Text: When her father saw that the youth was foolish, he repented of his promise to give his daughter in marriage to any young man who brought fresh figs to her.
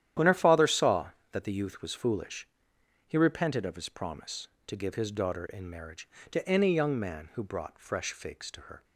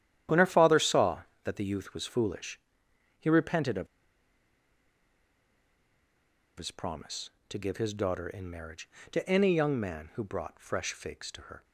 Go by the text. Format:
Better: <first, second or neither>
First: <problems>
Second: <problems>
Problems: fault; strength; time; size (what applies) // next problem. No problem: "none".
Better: first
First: starts louder than the rest; strong; until 1.3 s; 11 dB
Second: starts louder than the rest; strong; until 1.5 s; 11 dB // pauses between "of" and "his"; strong; at 3.8 s; 2.7 s long